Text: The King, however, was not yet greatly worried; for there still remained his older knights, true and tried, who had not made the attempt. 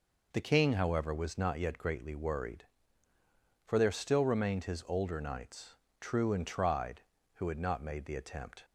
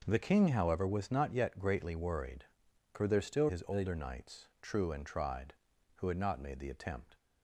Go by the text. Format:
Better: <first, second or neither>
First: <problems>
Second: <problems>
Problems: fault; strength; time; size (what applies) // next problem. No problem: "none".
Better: first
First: none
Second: skips "remained"; at 3.4 s